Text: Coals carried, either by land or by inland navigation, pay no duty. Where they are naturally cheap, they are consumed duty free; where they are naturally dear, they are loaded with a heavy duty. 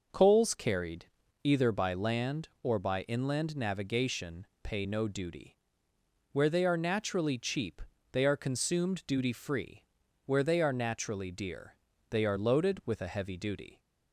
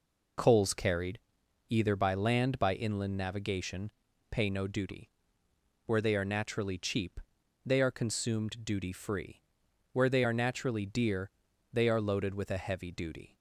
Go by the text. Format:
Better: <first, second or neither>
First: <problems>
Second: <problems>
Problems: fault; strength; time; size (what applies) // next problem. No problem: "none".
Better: first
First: none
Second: skips "or"; at 2.5 s